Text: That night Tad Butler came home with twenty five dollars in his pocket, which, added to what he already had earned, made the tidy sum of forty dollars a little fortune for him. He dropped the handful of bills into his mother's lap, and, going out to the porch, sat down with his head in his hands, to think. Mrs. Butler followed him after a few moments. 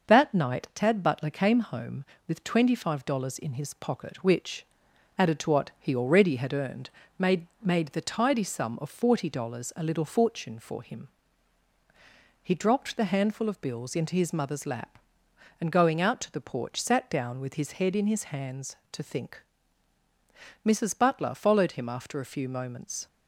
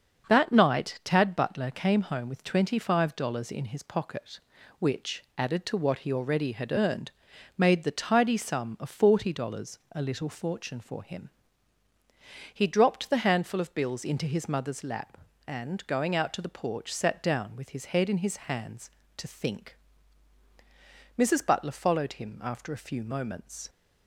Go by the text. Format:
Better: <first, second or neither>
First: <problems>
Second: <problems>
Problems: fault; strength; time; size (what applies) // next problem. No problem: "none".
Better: second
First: starts louder than the rest; noticeable; until 1.1 s; 6 dB // says "made" twice; at 7.6 s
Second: starts louder than the rest; until 1.3 s; 6.5 dB